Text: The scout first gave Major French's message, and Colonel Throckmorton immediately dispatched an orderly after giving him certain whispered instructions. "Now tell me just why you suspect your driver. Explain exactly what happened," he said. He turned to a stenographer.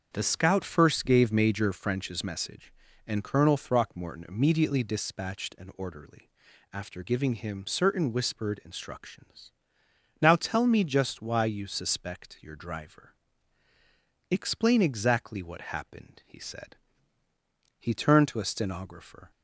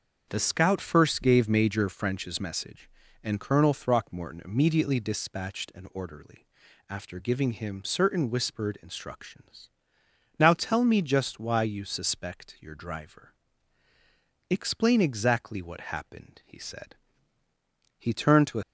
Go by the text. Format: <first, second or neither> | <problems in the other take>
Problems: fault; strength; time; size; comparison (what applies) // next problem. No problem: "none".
first | starts louder than the rest; until 1.3 s; 6.5 dB; also in the first // pauses between "orderly" and "after"; at 6.4 s; 0.44 s long; also in the first // stops before "stenographer"; at 18.6 s